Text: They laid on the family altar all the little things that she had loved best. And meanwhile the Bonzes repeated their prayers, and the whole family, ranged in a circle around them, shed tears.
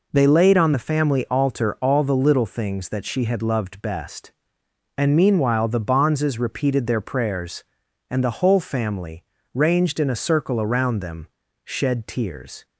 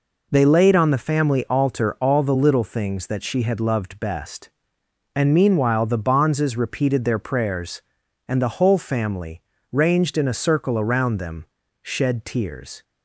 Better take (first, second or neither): neither